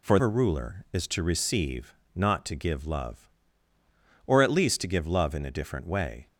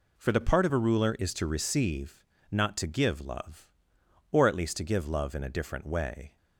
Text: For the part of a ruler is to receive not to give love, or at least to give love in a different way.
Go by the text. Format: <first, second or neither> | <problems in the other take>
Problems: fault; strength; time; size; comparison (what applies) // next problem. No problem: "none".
second | skips "the part of"; at 0.1 s // pauses between "receive" and "not"; slight; at 1.9 s; 0.18 s long; slight in the second